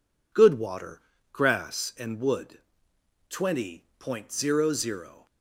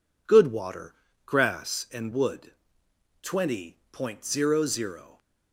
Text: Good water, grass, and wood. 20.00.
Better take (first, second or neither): neither